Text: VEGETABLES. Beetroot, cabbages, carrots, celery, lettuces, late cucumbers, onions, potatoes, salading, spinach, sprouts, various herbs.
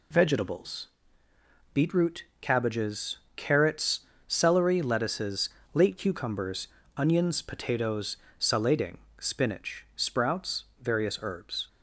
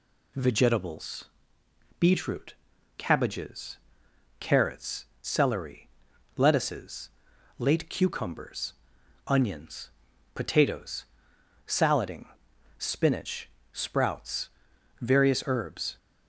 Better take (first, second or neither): neither